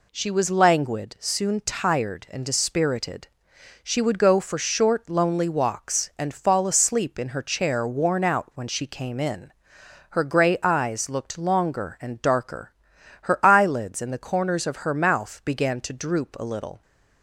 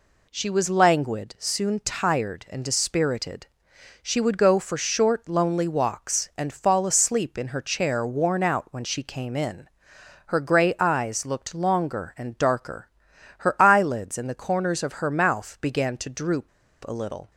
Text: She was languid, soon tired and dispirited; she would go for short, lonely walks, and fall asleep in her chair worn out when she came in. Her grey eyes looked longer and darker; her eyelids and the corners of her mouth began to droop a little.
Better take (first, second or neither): first